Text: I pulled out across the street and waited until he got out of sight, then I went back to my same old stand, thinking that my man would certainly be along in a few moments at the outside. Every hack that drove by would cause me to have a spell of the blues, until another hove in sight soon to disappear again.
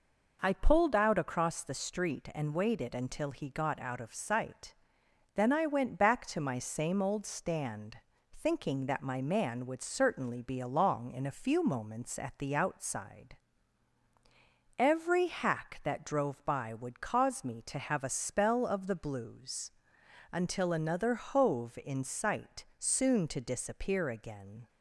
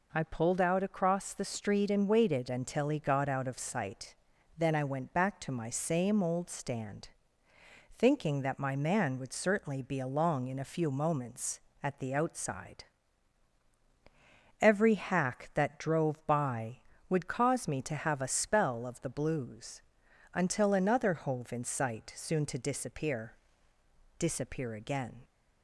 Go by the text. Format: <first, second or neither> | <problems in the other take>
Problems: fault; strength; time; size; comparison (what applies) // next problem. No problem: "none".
first | says "disappear" twice; at 24.1 s